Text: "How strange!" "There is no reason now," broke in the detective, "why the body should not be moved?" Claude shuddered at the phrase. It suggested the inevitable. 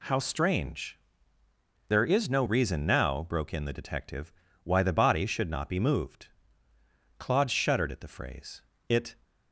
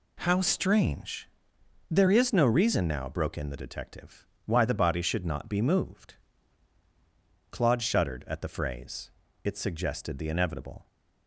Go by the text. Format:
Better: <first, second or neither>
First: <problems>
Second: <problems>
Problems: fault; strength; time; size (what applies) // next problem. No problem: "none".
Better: second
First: stops before "suggested the inevitable"; at 9.2 s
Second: none